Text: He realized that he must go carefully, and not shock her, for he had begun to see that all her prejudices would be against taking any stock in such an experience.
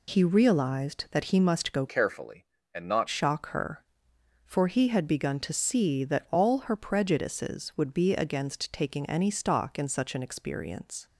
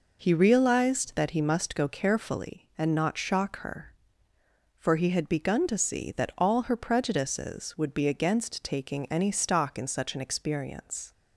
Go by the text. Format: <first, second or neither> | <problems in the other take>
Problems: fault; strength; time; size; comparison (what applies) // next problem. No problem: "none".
second | changes voice from "carefully" to "not"; from 1.8 to 3.0 s; 1.2 s long